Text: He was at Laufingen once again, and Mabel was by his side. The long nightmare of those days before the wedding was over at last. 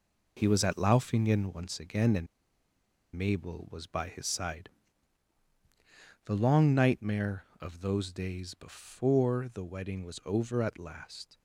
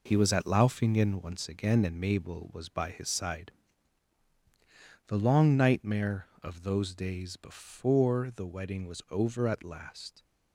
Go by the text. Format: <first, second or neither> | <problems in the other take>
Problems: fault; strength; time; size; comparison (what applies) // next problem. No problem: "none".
second | pauses between "and" and "Mabel"; noticeable; at 2.2 s; 0.89 s long